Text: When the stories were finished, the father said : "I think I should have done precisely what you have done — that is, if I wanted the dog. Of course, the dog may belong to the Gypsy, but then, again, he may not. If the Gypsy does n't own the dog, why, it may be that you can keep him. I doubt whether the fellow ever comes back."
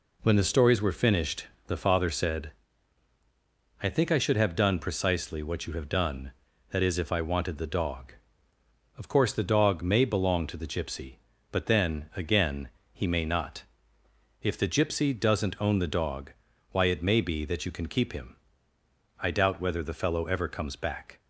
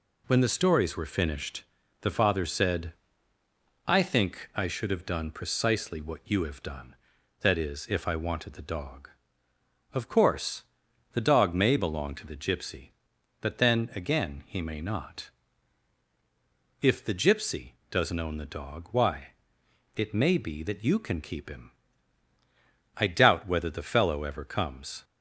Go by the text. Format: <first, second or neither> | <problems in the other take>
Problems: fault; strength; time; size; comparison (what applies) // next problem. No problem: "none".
first | stops before "back"; at 25.0 s